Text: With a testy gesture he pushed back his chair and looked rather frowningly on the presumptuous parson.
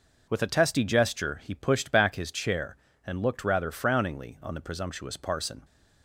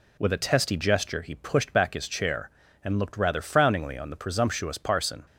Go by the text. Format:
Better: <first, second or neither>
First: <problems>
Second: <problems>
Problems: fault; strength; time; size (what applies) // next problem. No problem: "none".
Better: neither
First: none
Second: none